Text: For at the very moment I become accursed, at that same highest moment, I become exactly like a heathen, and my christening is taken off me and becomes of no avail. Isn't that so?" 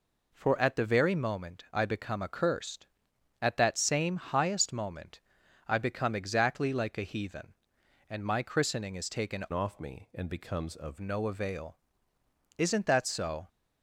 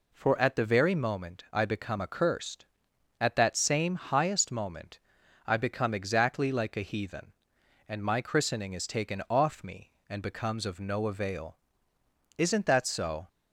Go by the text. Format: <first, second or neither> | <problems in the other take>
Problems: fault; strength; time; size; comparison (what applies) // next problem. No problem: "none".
second | changes voice from "off" to "of"; from 9.5 to 10.9 s; 1.4 s long